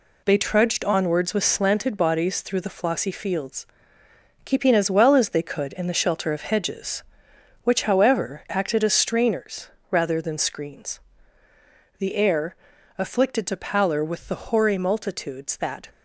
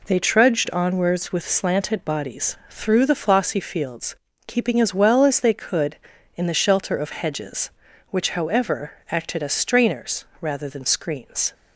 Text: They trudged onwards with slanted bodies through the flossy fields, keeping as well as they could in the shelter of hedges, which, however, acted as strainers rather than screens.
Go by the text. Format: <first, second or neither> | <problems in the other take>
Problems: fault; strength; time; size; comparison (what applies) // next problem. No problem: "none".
second | pauses between "strainers" and "rather"; slight; at 9.6 s; 0.22 s long; slight in the second // goes on to say "The air afflicted to pallor with the hoary multitudes that"; strong; from 11.9 s on; 3.9 s long